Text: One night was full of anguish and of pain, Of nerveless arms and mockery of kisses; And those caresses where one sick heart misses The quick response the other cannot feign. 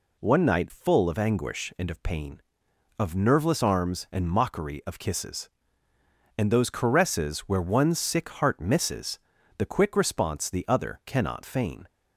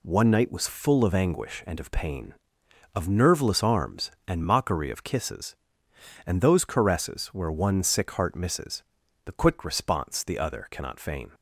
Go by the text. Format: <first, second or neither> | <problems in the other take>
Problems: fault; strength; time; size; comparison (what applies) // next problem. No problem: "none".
second | skips "was"; at 0.7 s // pauses between "misses" and "The"; at 9.1 s; 0.40 s long; also in the second